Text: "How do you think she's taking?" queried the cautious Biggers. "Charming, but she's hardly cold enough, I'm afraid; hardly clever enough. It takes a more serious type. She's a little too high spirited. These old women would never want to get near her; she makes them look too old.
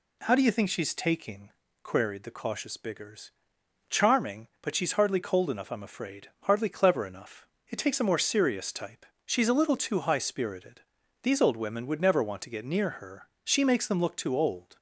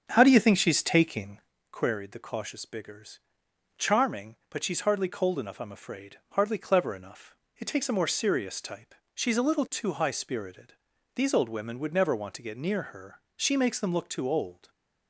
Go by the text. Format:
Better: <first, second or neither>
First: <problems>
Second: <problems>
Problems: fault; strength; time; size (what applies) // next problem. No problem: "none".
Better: first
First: none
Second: starts louder than the rest; strong; until 1.6 s; 7.5 dB